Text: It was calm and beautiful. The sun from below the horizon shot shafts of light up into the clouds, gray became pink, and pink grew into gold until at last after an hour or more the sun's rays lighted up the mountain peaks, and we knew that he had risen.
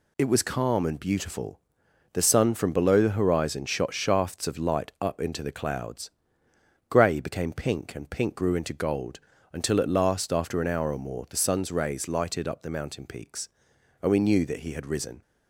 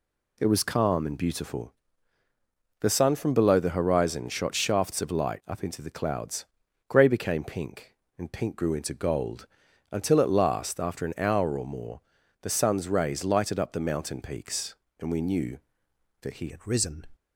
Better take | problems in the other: first | pauses between "gold" and "until"; at 9.4 s; 0.42 s long; slight in the first // pauses between "more" and "the"; at 12.0 s; 0.40 s long // changes voice at "had"; from 16.4 s on; 0.6 s long

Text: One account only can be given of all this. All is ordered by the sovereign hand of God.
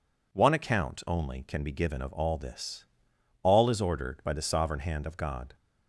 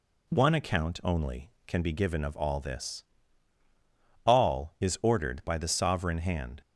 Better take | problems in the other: first | stops before "of God"; at 6.6 s

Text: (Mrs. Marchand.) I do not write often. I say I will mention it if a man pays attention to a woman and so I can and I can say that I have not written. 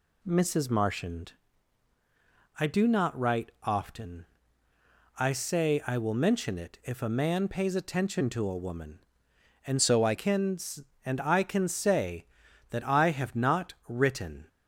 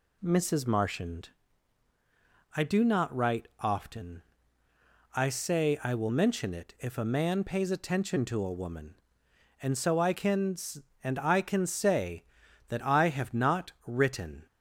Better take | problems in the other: second | changes voice from "so" to "I"; from 9.7 to 10.1 s; 0.4 s long

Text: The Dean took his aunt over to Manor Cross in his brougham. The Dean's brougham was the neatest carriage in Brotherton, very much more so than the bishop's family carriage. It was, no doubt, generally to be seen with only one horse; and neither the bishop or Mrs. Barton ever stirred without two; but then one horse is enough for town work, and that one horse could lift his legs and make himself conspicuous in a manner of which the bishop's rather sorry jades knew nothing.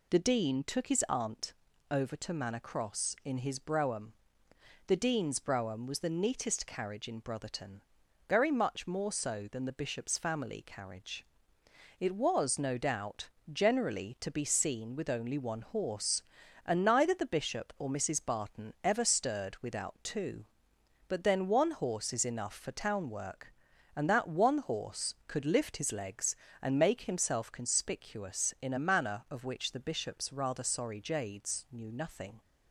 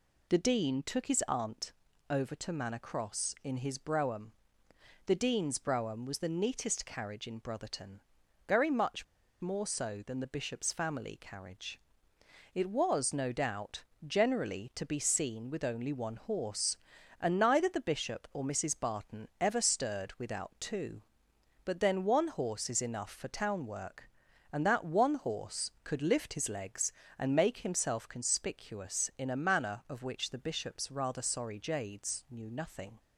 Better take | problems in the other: first | pauses between "aunt" and "over"; at 1.7 s; 0.38 s long; also in the first // pauses between "much" and "more"; slight; at 9.0 s; 0.36 s long

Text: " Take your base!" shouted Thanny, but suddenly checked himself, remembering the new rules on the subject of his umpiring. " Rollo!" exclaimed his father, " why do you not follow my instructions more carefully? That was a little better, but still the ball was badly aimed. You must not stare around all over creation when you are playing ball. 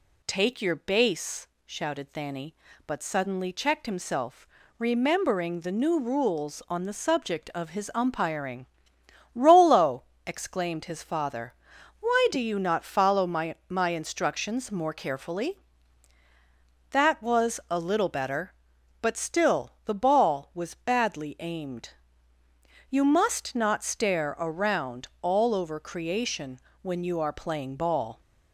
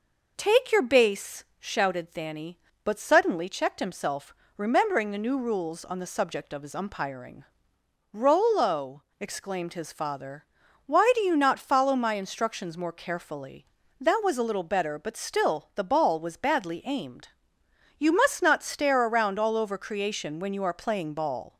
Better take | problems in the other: second | says "my" twice; at 13.6 s // pauses between "creation" and "when"; slight; at 26.6 s; 0.22 s long

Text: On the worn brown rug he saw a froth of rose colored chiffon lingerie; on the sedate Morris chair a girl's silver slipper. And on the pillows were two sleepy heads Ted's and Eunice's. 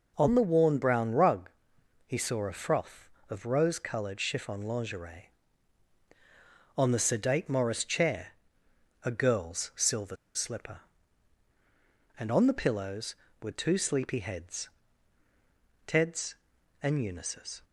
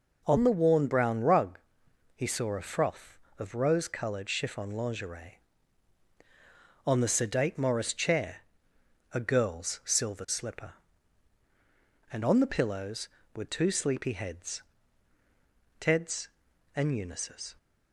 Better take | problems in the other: second | pauses between "rug" and "he"; noticeable; at 1.4 s; 0.56 s long; noticeable in the second // pauses between "chair" and "a"; noticeable; at 8.2 s; 0.76 s long; noticeable in the second // pauses between "silver" and "slipper"; slight; at 10.1 s; 0.19 s long // pauses between "heads" and "Ted's"; at 14.6 s; 1.1 s long; also in the second

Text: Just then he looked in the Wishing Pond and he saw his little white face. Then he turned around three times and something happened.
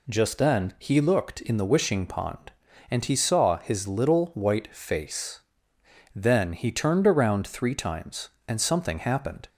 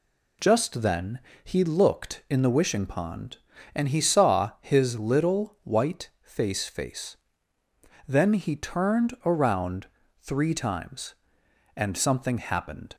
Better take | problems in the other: first | pauses between "then" and "he"; slight; at 1.1 s; 0.24 s long // says "face" twice; at 6.6 s // pauses between "around" and "three"; slight; at 9.8 s; 0.34 s long

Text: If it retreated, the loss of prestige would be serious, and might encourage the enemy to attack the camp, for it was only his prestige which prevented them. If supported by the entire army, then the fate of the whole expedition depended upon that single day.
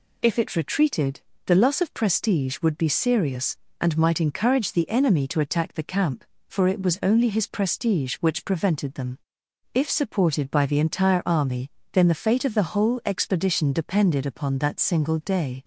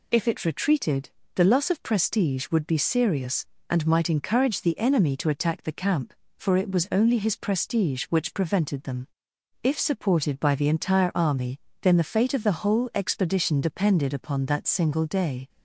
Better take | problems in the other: neither | none

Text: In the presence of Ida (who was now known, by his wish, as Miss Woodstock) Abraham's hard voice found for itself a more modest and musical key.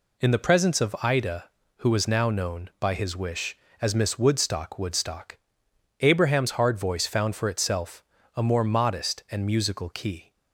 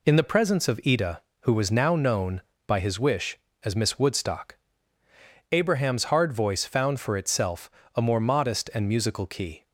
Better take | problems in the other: second | says "Woodstock" twice; at 4.7 s // pauses between "itself" and "a"; slight; at 8.0 s; 0.32 s long; slight in the second

